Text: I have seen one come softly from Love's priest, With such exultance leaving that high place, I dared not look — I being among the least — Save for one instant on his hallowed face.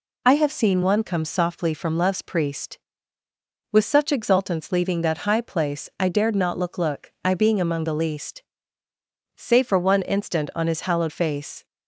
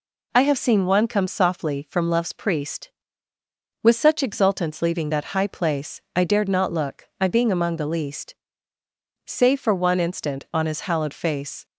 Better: second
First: says "look" twice; at 6.7 s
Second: none

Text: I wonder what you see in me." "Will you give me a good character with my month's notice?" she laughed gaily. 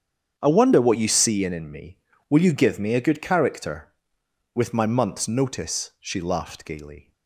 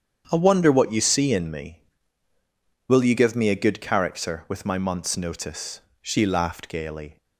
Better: second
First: starts louder than the rest; strong; until 1.4 s; 8.5 dB // says "in" twice; at 1.5 s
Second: starts louder than the rest; strong; until 1.3 s; 8 dB

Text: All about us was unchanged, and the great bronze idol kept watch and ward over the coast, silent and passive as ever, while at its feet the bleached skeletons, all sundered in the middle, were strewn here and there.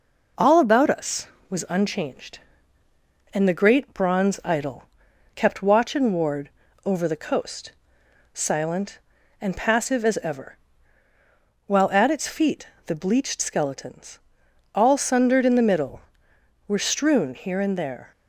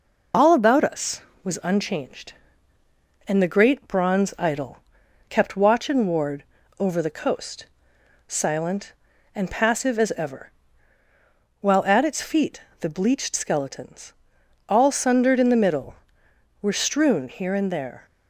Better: first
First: pauses between "idol" and "kept"; noticeable; at 4.8 s; 0.52 s long // pauses between "ward" and "over"; slight; at 6.4 s; 0.36 s long // pauses between "feet" and "the"; slight; at 12.6 s; 0.18 s long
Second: loses the start of "All"; at 0.3 s; 35 ms // pauses between "idol" and "kept"; noticeable; at 4.7 s; 0.52 s long // pauses between "ward" and "over"; slight; at 6.4 s; 0.36 s long // pauses between "feet" and "the"; slight; at 12.6 s; 0.18 s long

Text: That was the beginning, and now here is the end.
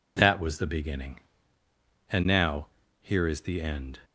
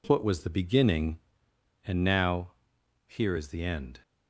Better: first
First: pauses between "now" and "here"; slight; at 2.6 s; 0.34 s long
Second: says "What" for "That"; at 0.0 s // pauses between "now" and "here"; noticeable; at 2.5 s; 0.54 s long

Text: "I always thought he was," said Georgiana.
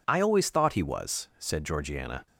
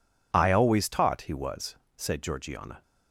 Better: first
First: none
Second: says "taught" for "thought"; at 0.8 s

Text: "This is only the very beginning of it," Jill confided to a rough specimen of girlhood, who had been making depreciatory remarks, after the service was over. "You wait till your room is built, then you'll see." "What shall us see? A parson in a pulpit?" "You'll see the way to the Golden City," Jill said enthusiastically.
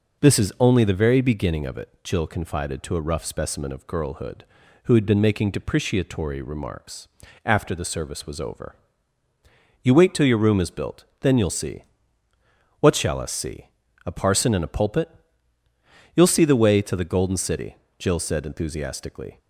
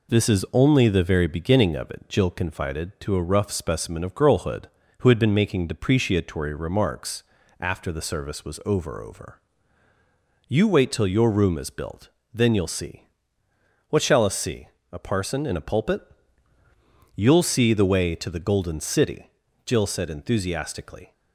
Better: first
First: none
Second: says "over" twice; at 9.0 s

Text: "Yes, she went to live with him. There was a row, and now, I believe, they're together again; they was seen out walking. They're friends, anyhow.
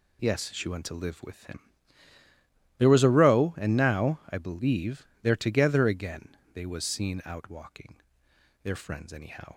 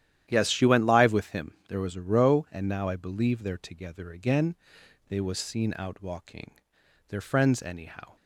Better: first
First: none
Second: starts louder than the rest; strong; until 1.3 s; 11 dB // skips "to"; at 0.8 s

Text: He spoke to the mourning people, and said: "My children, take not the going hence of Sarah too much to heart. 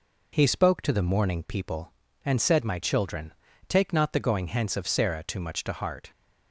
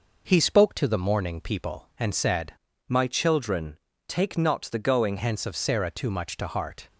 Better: first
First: none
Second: changes voice from "My" to "going"; from 2.8 to 5.1 s; 2.3 s long

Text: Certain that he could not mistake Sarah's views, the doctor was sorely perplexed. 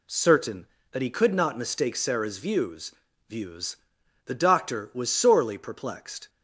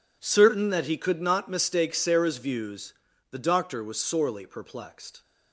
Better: second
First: says "views" twice; at 3.2 s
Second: none

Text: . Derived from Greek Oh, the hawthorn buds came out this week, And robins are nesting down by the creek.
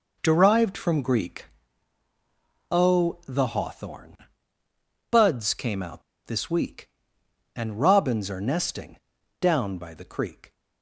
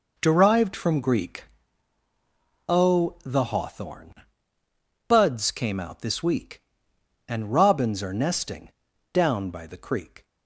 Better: second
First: pauses between "Greek" and "Oh"; at 1.4 s; 1.2 s long // pauses between "hawthorn" and "buds"; noticeable; at 4.1 s; 0.94 s long // pauses between "out" and "this"; slight; at 6.0 s; 0.24 s long // pauses between "nesting" and "down"; at 8.9 s; 0.40 s long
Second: pauses between "Greek" and "Oh"; at 1.4 s; 1.2 s long // pauses between "hawthorn" and "buds"; noticeable; at 4.1 s; 0.94 s long // pauses between "nesting" and "down"; at 8.7 s; 0.40 s long

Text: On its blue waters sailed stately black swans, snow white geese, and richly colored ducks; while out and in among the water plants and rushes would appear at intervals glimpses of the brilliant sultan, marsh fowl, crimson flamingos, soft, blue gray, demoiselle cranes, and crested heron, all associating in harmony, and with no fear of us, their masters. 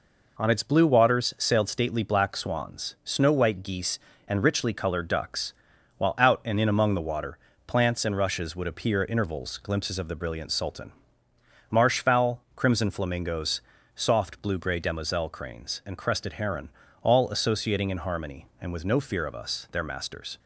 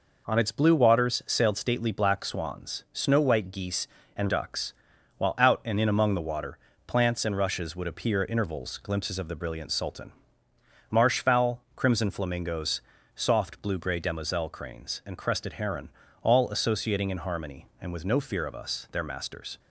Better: first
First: pauses between "water" and "plants"; slight; at 7.3 s; 0.30 s long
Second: skips "richly colored"; at 4.2 s // pauses between "water" and "plants"; slight; at 6.5 s; 0.30 s long

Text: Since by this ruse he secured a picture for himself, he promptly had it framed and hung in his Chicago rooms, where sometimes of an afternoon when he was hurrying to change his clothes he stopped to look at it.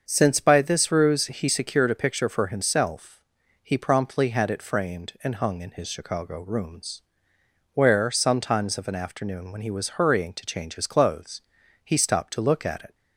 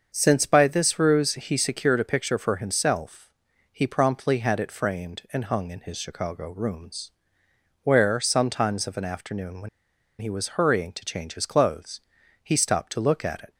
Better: first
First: starts louder than the rest; until 1.0 s; 6.5 dB // pauses between "clothes" and "he"; at 11.4 s; 0.44 s long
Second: starts louder than the rest; until 1.1 s; 6.5 dB // pauses between "when" and "he"; noticeable; at 9.6 s; 0.50 s long // pauses between "clothes" and "he"; at 11.9 s; 0.44 s long

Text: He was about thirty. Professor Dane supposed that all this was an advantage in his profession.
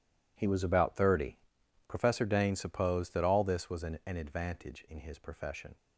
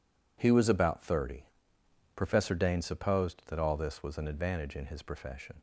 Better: second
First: says "an" twice; at 4.0 s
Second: none

